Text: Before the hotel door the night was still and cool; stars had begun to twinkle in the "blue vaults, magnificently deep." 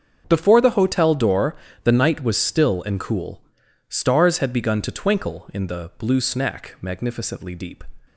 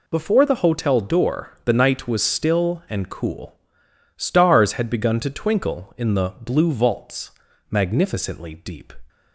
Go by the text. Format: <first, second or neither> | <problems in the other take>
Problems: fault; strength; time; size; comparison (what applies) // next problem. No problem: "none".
second | starts louder than the rest; until 1.2 s; 7 dB // pauses between "door" and "the"; slight; at 1.5 s; 0.28 s long // says "snack" for "vaults"; at 6.1 s